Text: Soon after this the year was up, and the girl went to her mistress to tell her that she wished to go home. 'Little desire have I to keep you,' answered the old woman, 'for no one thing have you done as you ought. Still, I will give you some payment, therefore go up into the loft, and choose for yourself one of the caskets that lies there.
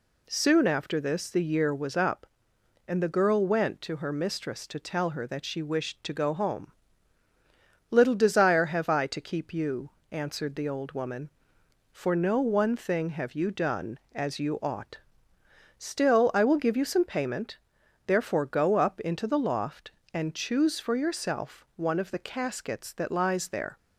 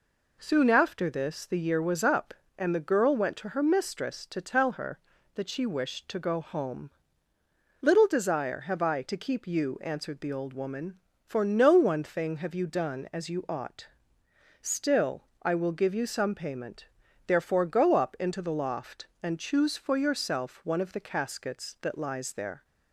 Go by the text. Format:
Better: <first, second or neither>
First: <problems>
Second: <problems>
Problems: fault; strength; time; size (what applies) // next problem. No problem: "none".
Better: neither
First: none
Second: none